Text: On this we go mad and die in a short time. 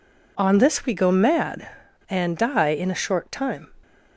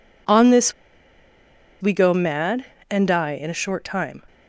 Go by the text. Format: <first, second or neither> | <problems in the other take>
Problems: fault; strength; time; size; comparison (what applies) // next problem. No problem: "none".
first | pauses between "this" and "we"; at 0.7 s; 1.0 s long